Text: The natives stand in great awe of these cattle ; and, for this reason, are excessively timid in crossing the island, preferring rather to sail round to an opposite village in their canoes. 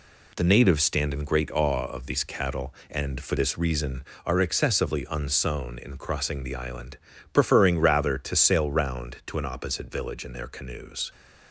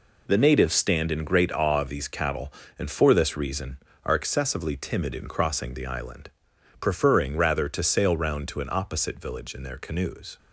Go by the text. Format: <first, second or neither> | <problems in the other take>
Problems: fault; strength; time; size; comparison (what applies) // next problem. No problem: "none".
second | says "unsown" for "timid"; at 5.1 s